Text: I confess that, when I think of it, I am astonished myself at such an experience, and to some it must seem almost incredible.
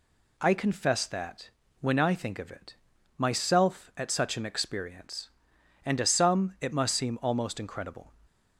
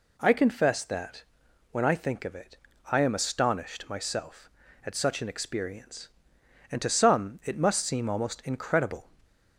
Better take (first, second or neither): second